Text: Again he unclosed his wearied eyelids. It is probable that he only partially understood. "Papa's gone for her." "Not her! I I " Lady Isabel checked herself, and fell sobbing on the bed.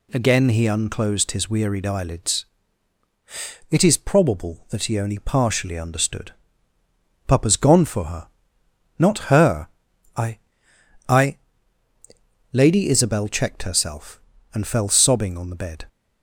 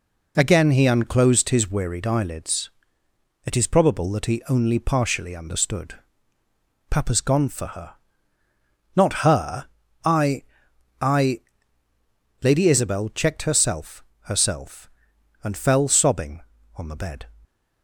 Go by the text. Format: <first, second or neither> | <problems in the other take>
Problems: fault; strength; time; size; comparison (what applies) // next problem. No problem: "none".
first | pauses between "I" and "I"; noticeable; at 10.4 s; 0.58 s long; noticeable in the first // says "herself" twice; at 14.2 s